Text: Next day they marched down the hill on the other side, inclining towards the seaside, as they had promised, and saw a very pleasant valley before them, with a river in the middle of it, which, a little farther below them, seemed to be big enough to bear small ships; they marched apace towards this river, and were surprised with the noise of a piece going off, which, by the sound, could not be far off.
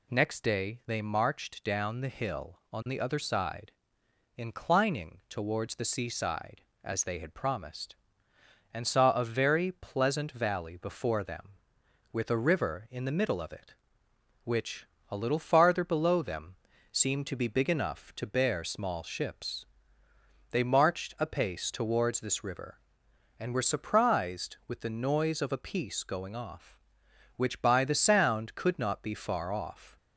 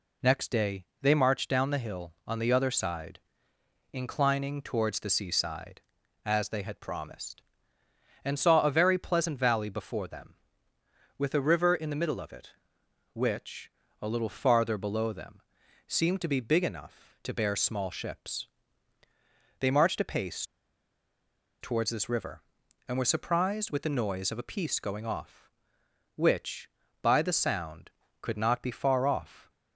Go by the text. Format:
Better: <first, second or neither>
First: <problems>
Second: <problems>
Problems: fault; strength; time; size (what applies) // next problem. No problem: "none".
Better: first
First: none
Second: pauses between "day" and "they"; slight; at 0.8 s; 0.16 s long // pauses between "apace" and "towards"; at 20.4 s; 1.1 s long